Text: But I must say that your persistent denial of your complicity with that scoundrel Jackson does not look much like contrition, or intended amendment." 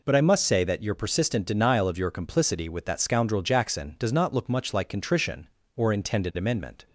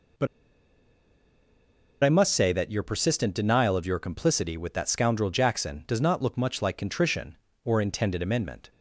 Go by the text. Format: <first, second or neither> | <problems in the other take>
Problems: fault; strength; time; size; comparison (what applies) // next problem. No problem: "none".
first | pauses between "But" and "I"; strong; at 0.2 s; 1.7 s long